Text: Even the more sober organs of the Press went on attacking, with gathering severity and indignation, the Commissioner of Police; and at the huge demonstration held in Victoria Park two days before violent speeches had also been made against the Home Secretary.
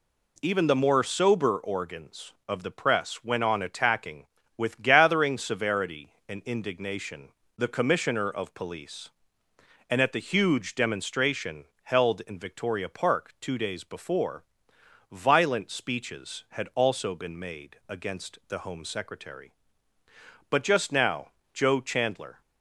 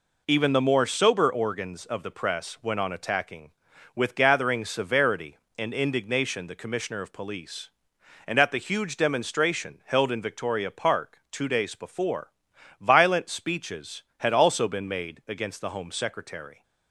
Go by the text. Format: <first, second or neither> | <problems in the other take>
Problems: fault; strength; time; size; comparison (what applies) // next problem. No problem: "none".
second | pauses between "demonstration" and "held"; slight; at 11.6 s; 0.20 s long // pauses between "before" and "violent"; noticeable; at 14.4 s; 0.68 s long; noticeable in the second // goes on to say "But just now Joe Chandler"; strong; from 20.5 s on; 1.9 s long